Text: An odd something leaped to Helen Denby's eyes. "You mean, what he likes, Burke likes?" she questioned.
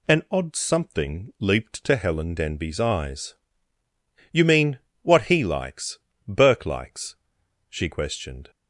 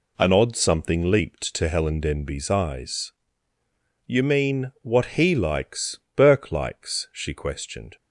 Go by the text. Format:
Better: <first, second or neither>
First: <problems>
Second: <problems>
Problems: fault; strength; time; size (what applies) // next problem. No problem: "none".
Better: first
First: none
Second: gets quieter; strong; throughout; 7.5 dB